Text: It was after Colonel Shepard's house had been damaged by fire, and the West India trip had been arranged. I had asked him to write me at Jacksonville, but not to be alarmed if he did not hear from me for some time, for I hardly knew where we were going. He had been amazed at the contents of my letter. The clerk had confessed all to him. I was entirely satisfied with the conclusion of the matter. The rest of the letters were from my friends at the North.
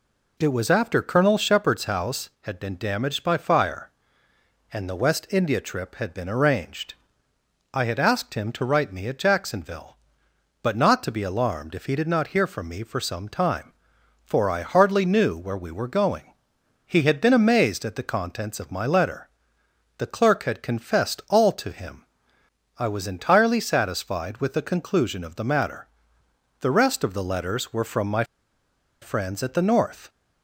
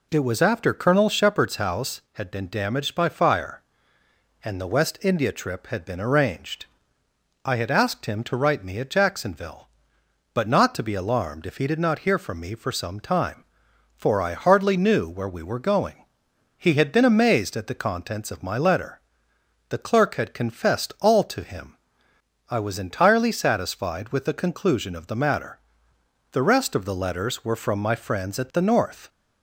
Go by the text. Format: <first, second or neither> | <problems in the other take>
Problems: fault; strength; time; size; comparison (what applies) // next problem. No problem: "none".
second | pauses between "my" and "friends"; noticeable; at 28.2 s; 0.78 s long